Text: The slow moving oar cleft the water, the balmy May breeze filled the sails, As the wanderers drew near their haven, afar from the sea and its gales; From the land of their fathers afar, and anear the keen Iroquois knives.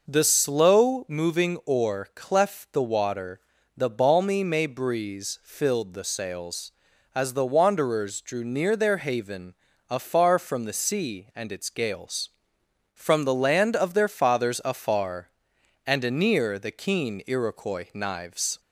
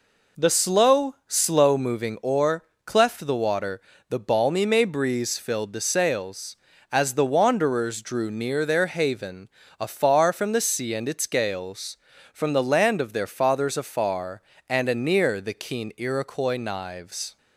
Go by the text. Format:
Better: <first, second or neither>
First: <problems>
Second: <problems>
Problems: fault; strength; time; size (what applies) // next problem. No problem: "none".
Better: first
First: none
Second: says "slow" twice; at 1.2 s // pauses between "oar" and "cleft"; slight; at 2.6 s; 0.20 s long